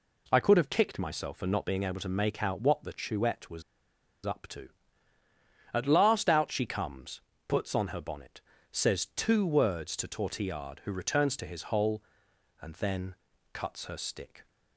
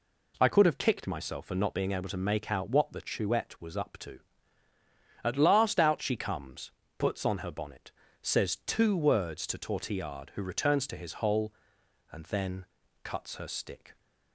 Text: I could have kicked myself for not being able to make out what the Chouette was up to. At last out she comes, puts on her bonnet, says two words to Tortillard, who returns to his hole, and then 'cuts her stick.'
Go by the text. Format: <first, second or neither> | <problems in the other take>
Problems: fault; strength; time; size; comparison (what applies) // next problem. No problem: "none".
second | pauses between "was" and "up"; noticeable; at 3.6 s; 0.63 s long // pauses between "then" and "cuts"; slight; at 13.1 s; 0.36 s long; slight in the second